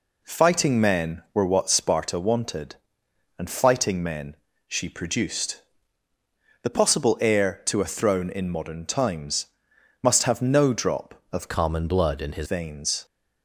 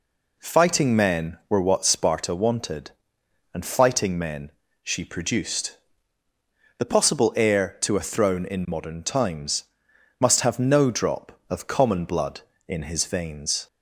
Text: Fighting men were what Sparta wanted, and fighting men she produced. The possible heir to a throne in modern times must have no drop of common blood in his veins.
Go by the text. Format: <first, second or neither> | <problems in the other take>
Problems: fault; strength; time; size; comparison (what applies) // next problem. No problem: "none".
second | pauses between "men" and "she"; slight; at 4.3 s; 0.32 s long; slight in the second // pauses between "times" and "must"; noticeable; at 9.4 s; 0.54 s long; noticeable in the second // changes voice from "common" to "his"; from 11.4 to 12.4 s; 1.0 s long